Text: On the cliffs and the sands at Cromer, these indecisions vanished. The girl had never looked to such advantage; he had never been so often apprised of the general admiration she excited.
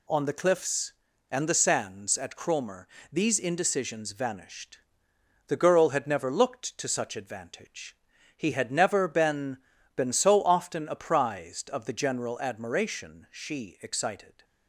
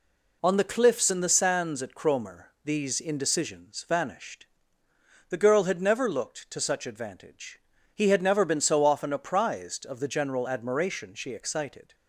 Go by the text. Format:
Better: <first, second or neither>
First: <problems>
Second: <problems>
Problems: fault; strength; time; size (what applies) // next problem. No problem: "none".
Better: second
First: says "been" twice; at 9.9 s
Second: none